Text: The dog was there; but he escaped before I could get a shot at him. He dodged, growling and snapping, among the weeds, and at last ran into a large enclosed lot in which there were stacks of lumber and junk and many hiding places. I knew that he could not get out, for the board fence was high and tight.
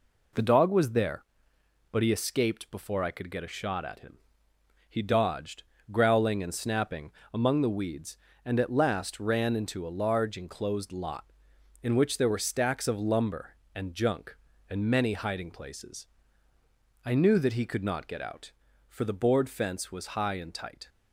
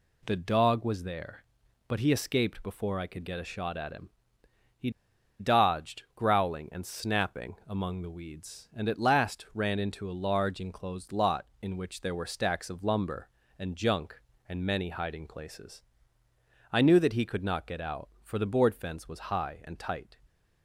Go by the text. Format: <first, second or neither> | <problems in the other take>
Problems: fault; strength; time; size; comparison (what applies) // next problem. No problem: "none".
first | pauses between "He" and "dodged"; noticeable; at 4.8 s; 0.49 s long